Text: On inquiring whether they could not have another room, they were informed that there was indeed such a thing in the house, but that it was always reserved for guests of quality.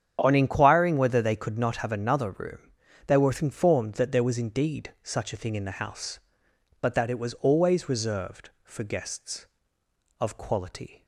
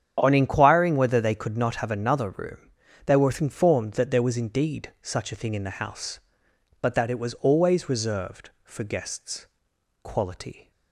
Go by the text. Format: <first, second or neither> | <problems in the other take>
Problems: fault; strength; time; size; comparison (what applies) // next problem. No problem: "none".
first | starts louder than the rest; strong; until 1.2 s; 9.5 dB; strong in the first // skips "of"; at 9.7 s